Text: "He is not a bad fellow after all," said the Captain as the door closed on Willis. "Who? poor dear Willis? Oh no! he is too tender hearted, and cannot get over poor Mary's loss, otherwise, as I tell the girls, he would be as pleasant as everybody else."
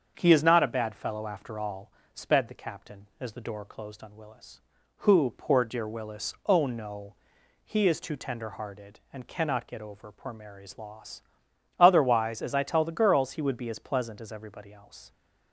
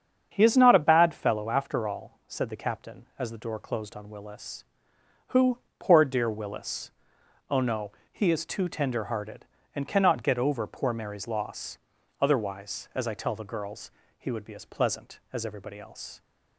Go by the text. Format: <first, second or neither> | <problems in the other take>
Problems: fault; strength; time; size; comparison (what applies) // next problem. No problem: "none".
second | starts louder than the rest; until 1.1 s; 7 dB; strong in the second // says "sped" for "said"; at 2.1 s